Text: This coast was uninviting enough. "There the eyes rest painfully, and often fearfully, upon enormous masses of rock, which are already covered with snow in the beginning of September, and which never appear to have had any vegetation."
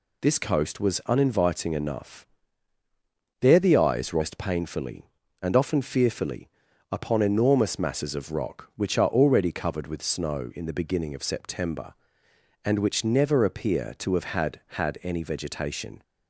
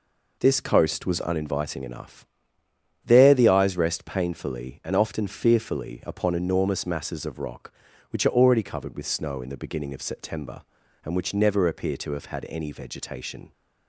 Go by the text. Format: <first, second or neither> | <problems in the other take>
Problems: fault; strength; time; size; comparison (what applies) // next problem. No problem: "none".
second | says "had" twice; at 14.6 s